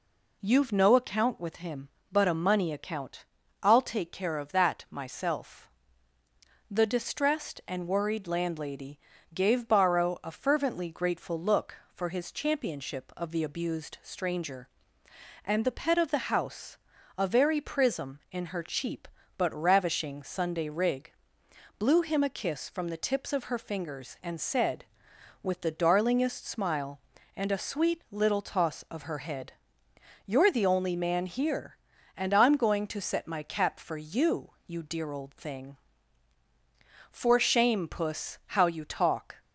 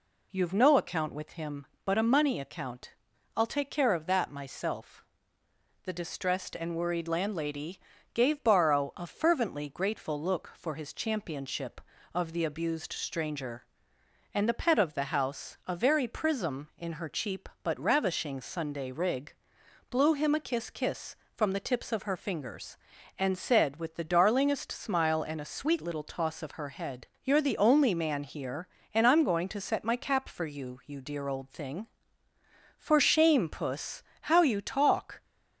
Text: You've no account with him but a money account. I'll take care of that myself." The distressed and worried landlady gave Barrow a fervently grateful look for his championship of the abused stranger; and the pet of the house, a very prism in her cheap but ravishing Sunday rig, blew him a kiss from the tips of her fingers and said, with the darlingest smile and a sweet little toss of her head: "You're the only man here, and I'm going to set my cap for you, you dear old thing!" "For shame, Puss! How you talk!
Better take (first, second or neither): first